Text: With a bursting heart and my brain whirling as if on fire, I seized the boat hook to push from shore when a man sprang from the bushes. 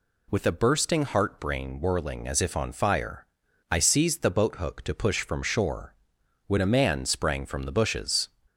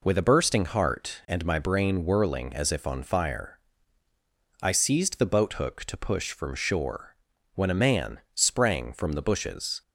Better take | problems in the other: second | skips "and my"; at 1.3 s // pauses between "shore" and "when"; noticeable; at 5.9 s; 0.50 s long; also in the second

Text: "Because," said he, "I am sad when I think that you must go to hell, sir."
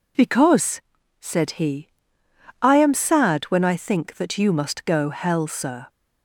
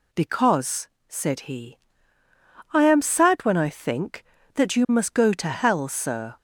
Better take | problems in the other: second | skips "to"; at 5.0 s

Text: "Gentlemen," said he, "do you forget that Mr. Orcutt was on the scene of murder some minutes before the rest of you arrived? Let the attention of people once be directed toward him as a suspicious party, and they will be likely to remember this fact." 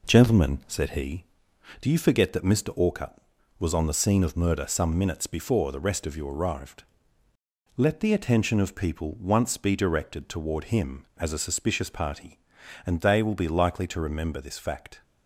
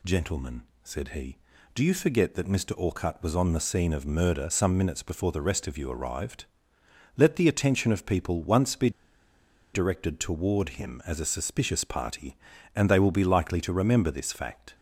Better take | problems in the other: first | pauses between "be" and "directed"; noticeable; at 8.8 s; 0.84 s long

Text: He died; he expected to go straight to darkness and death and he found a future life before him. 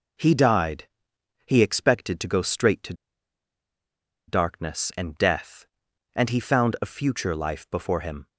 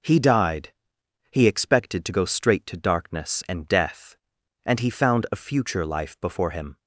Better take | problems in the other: second | pauses between "to" and "darkness"; strong; at 2.9 s; 1.3 s long

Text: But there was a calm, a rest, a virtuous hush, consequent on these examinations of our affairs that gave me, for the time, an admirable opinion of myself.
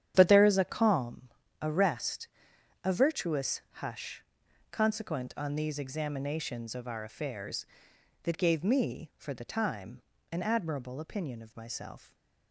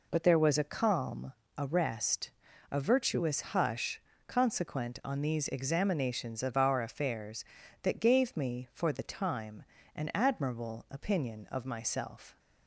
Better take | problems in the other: second | starts louder than the rest; strong; until 1.1 s; 9.5 dB // says "is" for "was"; at 0.4 s // stays silent after the last word; slight; from 11.9 s on; 0.6 s long

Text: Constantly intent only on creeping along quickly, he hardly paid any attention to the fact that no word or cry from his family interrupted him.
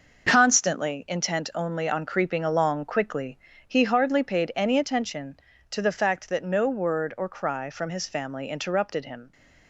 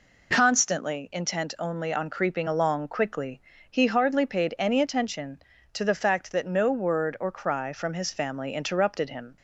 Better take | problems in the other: second | gets quieter; strong; throughout; 8 dB

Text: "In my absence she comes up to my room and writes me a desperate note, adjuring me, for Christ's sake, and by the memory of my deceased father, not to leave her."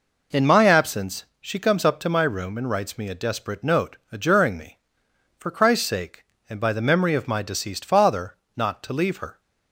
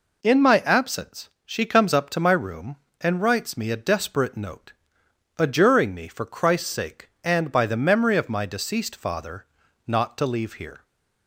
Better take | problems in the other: first | pauses between "absence" and "she"; slight; at 1.2 s; 0.16 s long; slight in the first // says "here" for "her"; at 10.5 s

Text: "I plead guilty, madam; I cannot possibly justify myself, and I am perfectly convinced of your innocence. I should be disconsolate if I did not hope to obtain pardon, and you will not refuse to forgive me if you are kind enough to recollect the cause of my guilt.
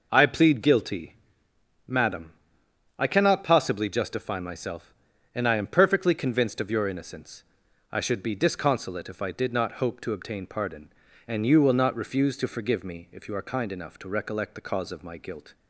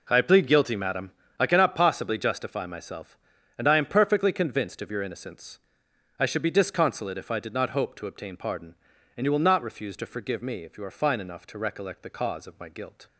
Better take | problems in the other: first | says "fine" for "kind"; at 10.9 s

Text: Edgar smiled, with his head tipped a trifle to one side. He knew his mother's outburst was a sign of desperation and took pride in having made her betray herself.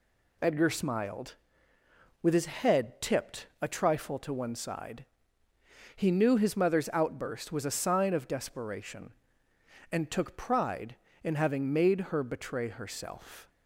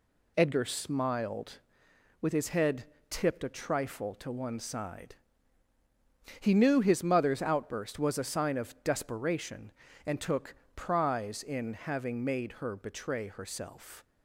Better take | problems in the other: first | pauses between "head" and "tipped"; slight; at 2.8 s; 0.26 s long // says "prize" for "pride"; at 10.7 s

